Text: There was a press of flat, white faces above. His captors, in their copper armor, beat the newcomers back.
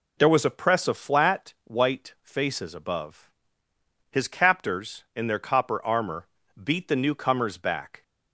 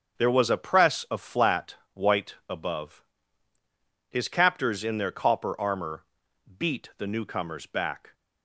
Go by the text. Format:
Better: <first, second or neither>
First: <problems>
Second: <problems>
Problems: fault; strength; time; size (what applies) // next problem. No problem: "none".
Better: first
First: none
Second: starts louder than the rest; until 1.2 s; 6.5 dB // skips "faces"; at 2.4 s